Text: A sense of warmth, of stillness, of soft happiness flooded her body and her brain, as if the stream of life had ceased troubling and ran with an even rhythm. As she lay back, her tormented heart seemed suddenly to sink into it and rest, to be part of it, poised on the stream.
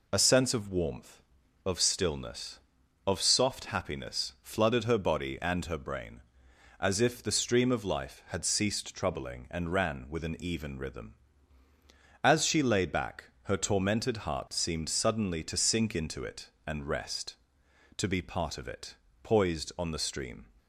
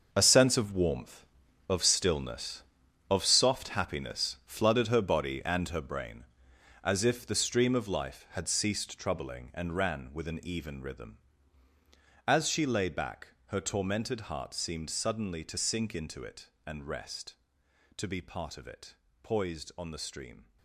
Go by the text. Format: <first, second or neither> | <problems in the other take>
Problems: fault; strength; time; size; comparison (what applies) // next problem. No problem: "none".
first | gets quieter; strong; throughout; 11.5 dB